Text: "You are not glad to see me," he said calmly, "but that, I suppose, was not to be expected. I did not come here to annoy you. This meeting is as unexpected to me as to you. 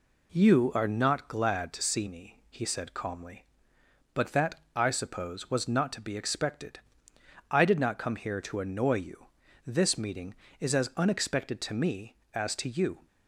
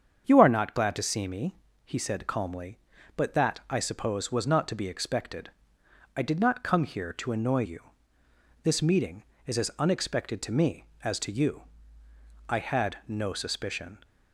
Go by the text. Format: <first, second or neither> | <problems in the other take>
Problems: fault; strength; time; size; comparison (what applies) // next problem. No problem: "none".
first | starts louder than the rest; strong; until 1.2 s; 7.5 dB // goes on to say "I had no suspicion"; from 12.4 s on; 1.5 s long